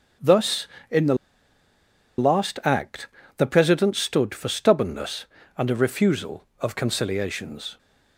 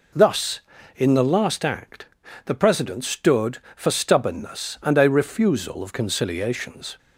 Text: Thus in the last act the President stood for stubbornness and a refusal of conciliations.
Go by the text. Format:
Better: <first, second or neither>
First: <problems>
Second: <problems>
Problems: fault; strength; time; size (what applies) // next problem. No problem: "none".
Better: second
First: starts louder than the rest; strong; until 2.4 s; 7.5 dB // pauses between "the" and "last"; at 1.1 s; 1.0 s long // pauses between "act" and "the"; slight; at 3.0 s; 0.30 s long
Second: pauses between "act" and "the"; at 2.0 s; 0.40 s long